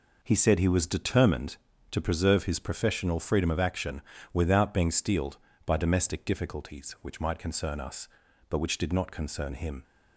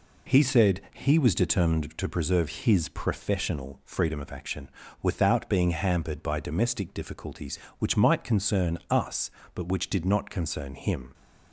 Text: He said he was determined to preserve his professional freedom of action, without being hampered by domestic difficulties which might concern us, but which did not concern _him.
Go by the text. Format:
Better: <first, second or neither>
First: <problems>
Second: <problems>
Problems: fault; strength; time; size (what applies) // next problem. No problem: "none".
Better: second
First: says "steeled" for "hampered"; at 4.8 s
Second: none